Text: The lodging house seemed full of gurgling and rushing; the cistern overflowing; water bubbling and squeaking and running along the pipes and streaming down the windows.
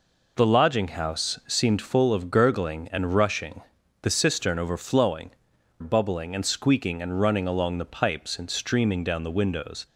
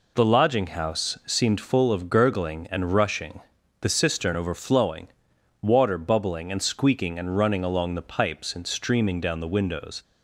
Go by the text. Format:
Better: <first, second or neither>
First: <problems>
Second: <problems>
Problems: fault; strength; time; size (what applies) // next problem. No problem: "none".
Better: second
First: skips "water"; at 5.5 s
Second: none